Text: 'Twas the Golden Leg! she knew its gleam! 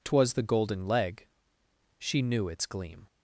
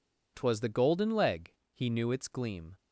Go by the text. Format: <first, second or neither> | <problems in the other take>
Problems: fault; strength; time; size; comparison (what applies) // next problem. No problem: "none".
first | says "he" for "she"; at 1.7 s